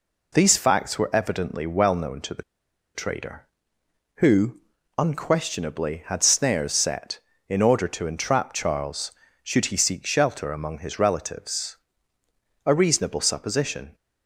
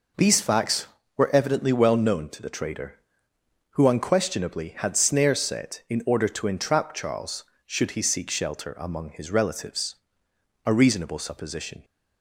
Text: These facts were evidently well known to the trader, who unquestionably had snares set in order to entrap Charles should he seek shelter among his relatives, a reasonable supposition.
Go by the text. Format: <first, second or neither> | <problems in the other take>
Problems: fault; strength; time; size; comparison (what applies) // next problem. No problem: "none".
second | pauses between "the" and "trader"; noticeable; at 2.4 s; 0.53 s long // pauses between "who" and "unquestionably"; at 4.5 s; 0.40 s long